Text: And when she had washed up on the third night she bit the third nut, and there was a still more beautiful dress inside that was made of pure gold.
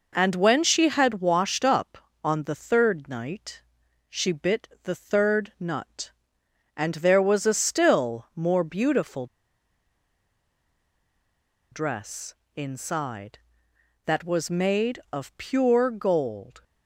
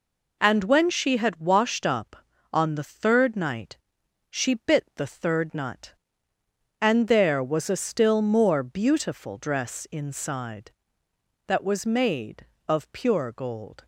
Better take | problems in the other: second | pauses between "night" and "she"; noticeable; at 3.6 s; 0.46 s long; noticeable in the second // pauses between "bit" and "the"; slight; at 4.6 s; 0.16 s long // pauses between "beautiful" and "dress"; strong; at 9.2 s; 2.4 s long // pauses between "dress" and "inside"; slight; at 12.3 s; 0.22 s long

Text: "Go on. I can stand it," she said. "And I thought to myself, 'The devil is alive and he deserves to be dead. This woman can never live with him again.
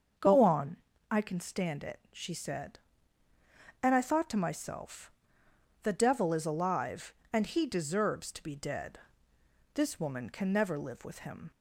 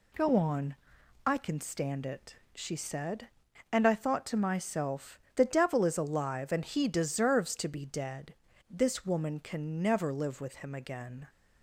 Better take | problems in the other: second | starts louder than the rest; until 1.5 s; 7 dB // stops before "again"; at 11.5 s

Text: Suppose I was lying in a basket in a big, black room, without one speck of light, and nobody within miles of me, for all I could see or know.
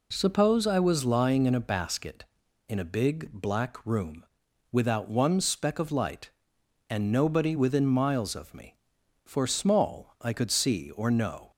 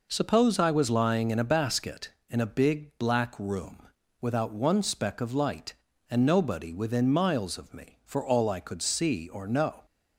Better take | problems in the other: second | says "small" for "all"; at 9.4 s

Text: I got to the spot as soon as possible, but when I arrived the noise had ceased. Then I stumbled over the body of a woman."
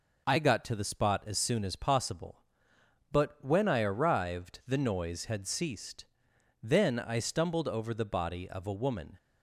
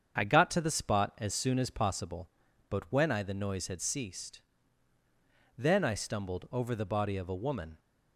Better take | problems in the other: first | starts louder than the rest; strong; until 1.2 s; 7 dB // skips "arrived"; at 3.2 s

